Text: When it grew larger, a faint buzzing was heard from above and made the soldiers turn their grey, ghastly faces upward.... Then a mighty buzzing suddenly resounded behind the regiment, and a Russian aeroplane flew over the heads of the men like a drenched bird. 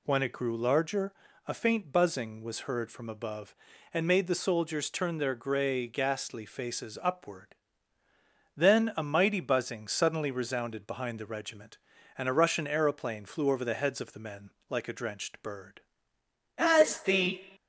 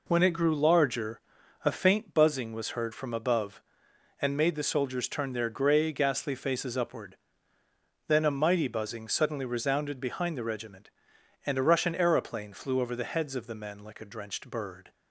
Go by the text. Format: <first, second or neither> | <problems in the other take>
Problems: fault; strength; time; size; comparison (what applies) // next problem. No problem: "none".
second | pauses between "men" and "like"; slight; at 14.5 s; 0.18 s long // goes on to say "As the"; noticeable; from 16.5 s on; 0.84 s long